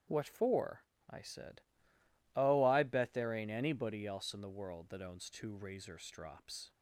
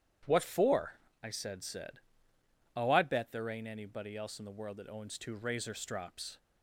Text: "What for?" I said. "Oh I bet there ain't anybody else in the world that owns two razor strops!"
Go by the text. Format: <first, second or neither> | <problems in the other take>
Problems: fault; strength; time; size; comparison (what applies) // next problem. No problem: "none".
first | starts louder than the rest; strong; until 1.5 s; 10 dB; strong in the first // says "said" twice; at 1.6 s